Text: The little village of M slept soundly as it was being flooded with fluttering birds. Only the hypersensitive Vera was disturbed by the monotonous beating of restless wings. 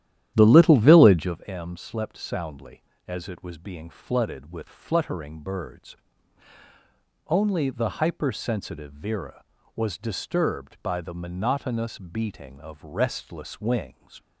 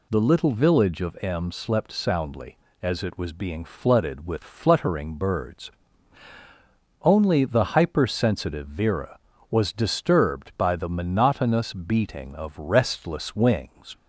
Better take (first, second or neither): second